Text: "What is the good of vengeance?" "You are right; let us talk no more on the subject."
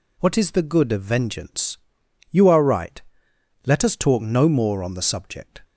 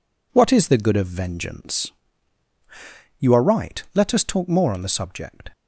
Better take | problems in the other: first | skips "no"; at 4.4 s

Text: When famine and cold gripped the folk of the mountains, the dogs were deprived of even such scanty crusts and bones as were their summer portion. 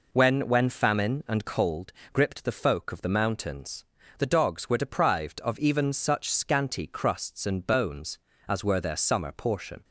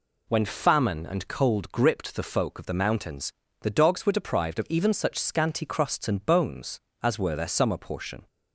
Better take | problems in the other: second | says "When" twice; at 0.4 s // pauses between "cold" and "gripped"; slight; at 1.9 s; 0.20 s long

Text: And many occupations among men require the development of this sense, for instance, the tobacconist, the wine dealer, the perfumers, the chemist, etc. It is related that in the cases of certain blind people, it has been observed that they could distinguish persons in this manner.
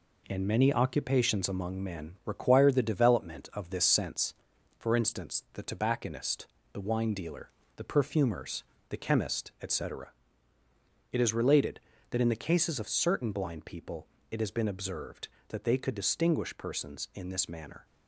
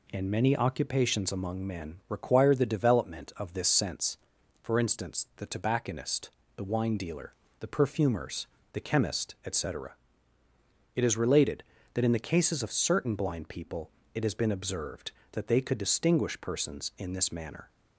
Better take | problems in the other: second | gets quieter; noticeable; throughout; 4.5 dB

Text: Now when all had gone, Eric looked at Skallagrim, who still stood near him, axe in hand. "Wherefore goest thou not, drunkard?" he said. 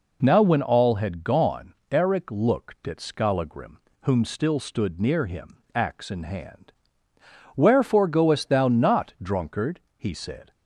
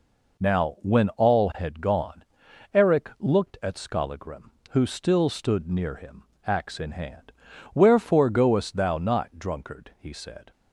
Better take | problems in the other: second | says "whom" for "who"; at 4.0 s

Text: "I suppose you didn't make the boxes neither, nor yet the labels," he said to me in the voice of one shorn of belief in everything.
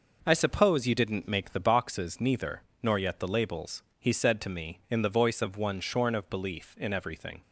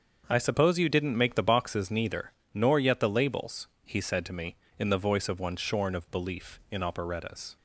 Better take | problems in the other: first | starts louder than the rest; until 1.2 s; 7 dB // says "operettas" for "everything"; at 6.8 s

